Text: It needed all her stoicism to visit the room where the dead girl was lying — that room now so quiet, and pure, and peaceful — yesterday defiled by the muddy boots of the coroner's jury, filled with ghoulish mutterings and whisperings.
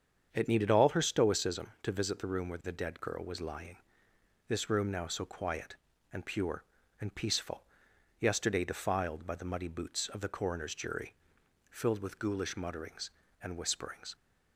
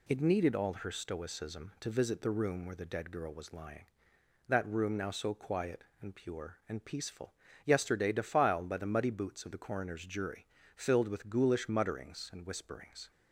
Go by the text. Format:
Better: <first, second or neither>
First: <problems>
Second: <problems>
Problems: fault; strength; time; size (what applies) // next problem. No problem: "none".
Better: second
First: starts louder than the rest; strong; until 1.3 s; 7.5 dB // says "this" for "that"; at 4.4 s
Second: none